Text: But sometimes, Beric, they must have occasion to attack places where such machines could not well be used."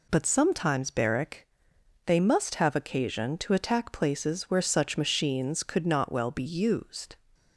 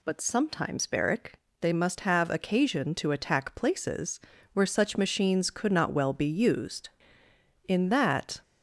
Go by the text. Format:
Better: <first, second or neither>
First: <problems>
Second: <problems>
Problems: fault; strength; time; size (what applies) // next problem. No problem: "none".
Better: first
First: none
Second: pauses between "places" and "where"; slight; at 4.1 s; 0.34 s long // goes on to say "In that"; noticeable; from 7.6 s on; 0.72 s long